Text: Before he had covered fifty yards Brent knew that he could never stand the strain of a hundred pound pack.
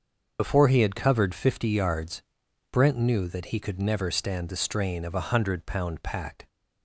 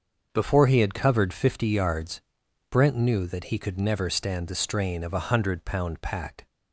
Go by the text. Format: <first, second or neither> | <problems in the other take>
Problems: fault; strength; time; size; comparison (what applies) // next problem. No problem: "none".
second | loses the start of "Before"; at 0.3 s; 65 ms // starts louder than the rest; until 1.4 s; 6.5 dB; also in the second // pauses between "yards" and "Brent"; noticeable; at 2.2 s; 0.50 s long; noticeable in the second